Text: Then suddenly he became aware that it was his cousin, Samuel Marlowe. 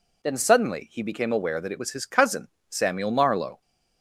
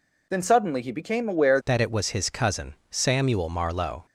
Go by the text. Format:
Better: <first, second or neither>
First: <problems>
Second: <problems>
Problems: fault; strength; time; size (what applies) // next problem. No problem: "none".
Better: first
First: none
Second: changes voice at "that"; from 1.6 s on; 2.4 s long